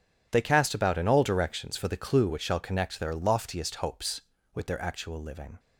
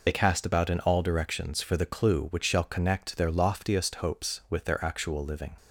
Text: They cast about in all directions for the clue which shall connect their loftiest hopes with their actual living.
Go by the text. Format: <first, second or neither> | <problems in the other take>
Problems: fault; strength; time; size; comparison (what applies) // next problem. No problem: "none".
first | loses the start of "They"; at 0.0 s; 35 ms